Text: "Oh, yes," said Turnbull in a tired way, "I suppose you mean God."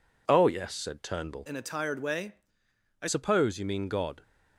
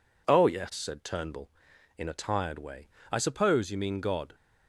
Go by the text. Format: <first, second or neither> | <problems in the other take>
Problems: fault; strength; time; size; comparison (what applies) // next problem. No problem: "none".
second | changes voice from "in" to "I"; from 1.4 to 3.0 s; 1.6 s long